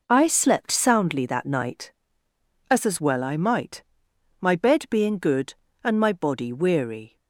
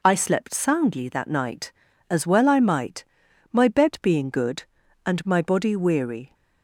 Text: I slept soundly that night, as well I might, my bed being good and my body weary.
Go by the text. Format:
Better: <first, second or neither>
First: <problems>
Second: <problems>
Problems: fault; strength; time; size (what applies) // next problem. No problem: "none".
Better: second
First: says "as" twice; at 2.8 s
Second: none